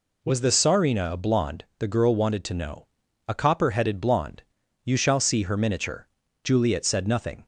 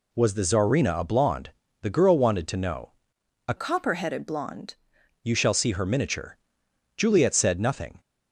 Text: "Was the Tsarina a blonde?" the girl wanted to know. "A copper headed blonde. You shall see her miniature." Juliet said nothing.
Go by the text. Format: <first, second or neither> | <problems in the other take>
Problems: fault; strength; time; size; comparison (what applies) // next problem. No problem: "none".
first | changes voice from "copper" to "blonde"; from 3.5 to 4.7 s; 1.2 s long